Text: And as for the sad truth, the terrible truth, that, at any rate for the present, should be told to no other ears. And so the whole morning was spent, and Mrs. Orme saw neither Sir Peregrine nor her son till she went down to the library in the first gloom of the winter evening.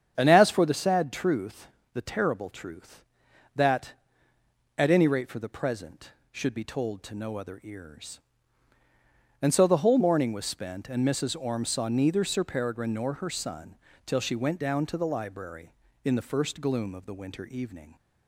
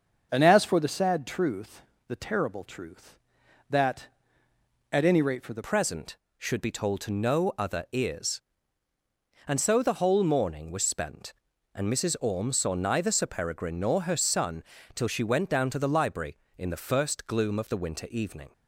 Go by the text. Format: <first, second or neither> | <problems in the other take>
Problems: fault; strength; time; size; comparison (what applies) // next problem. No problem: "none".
first | starts louder than the rest; until 1.3 s; 6.5 dB; strong in the first // changes voice at "present"; from 5.6 s on; 12.8 s long // pauses between "son" and "till"; slight; at 14.6 s; 0.30 s long; slight in the first